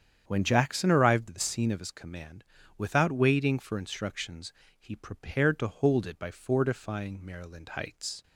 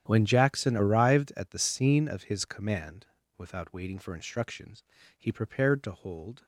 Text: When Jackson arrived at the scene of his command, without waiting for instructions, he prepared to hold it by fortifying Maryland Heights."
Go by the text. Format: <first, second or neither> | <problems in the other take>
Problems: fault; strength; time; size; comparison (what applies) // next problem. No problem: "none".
first | starts louder than the rest; strong; until 1.0 s; 10 dB; strong in the first // stops before "it by fortifying Maryland Heights"; at 6.4 s